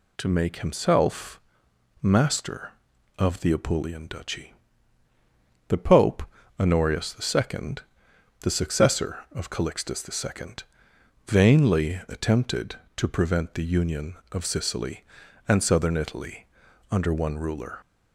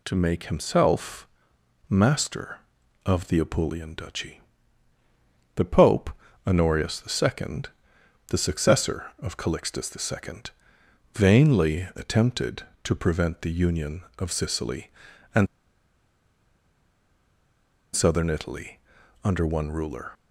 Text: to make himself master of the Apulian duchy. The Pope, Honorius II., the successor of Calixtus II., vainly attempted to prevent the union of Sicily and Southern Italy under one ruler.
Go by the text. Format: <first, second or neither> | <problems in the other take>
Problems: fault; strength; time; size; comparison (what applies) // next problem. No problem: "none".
first | pauses between "himself" and "master"; noticeable; at 1.2 s; 0.62 s long; noticeable in the first // pauses between "and" and "Southern"; strong; at 15.4 s; 2.4 s long // pauses between "Italy" and "under"; at 18.7 s; 0.44 s long; also in the first